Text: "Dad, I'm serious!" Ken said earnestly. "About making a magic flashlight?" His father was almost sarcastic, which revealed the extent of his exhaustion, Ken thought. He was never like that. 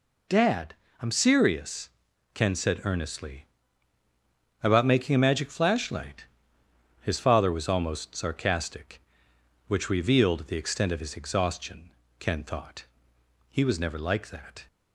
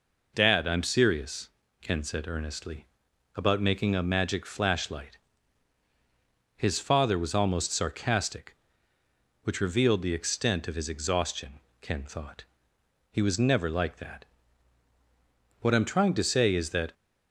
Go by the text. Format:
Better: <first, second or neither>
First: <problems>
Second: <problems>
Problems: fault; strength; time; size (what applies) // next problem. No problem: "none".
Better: first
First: none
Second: goes on to say "What I'm trying to say is that"; from 15.6 s on; 1.3 s long